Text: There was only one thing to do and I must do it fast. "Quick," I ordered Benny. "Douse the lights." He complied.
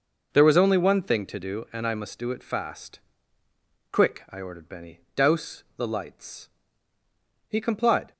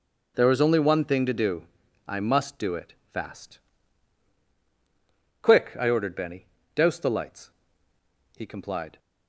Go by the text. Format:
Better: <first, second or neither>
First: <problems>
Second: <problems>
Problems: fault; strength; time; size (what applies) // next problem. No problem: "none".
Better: first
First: none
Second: skips "and"; at 1.8 s // pauses between "it" and "fast"; slight; at 2.9 s; 0.18 s long